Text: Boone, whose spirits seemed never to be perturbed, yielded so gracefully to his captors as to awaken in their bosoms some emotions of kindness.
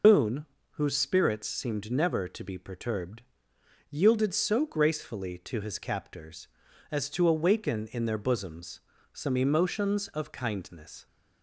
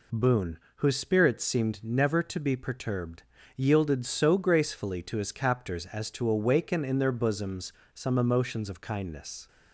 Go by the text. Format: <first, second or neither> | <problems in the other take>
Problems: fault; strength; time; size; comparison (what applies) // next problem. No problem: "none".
second | loses the start of "Boone"; at 0.0 s; 135 ms // pauses between "bosoms" and "some"; slight; at 8.7 s; 0.34 s long; slight in the second